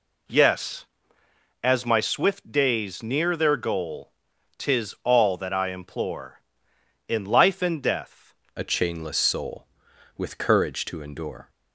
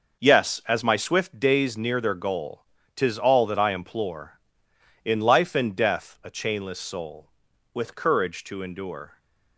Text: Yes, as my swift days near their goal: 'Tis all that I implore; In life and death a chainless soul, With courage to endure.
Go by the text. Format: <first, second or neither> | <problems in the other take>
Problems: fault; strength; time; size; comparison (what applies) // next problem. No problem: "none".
second | changes voice at "a"; from 8.5 s on; 2.9 s long